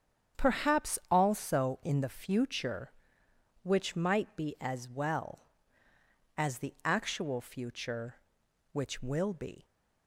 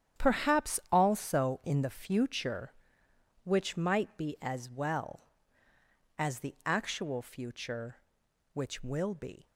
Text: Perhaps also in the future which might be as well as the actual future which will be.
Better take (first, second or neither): first